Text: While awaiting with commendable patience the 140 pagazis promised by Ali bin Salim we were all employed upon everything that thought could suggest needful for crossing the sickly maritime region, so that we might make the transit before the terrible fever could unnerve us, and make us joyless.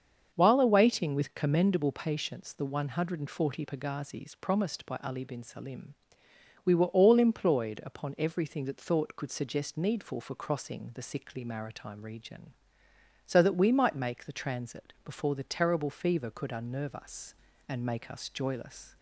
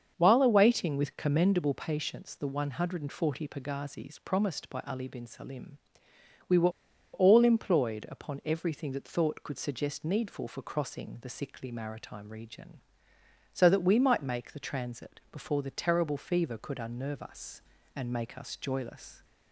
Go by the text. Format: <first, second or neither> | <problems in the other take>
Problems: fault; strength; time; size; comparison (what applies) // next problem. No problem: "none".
first | starts louder than the rest; until 1.1 s; 6.5 dB; also in the first // pauses between "Salim" and "we"; noticeable; at 5.7 s; 0.70 s long; noticeable in the first // pauses between "were" and "all"; at 6.7 s; 0.43 s long